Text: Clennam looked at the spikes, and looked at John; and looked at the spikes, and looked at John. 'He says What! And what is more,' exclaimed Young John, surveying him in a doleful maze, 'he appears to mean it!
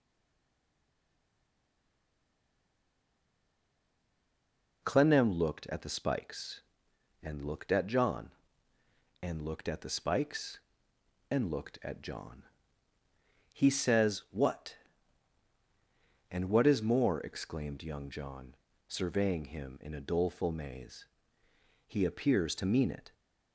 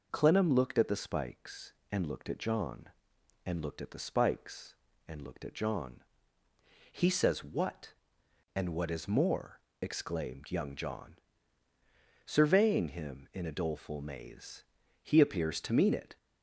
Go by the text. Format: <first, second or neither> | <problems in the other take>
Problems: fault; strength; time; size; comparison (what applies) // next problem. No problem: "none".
second | stays silent before the first word; strong; until 4.8 s; 4.8 s long